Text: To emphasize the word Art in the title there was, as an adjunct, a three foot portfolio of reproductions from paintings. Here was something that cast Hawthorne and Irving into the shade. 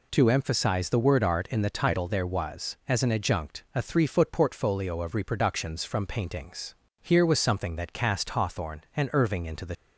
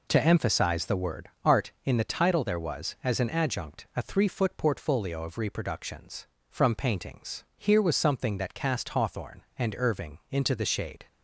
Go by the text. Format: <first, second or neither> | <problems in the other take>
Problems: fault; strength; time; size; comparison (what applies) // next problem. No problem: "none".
second | stops before "shade"; at 9.7 s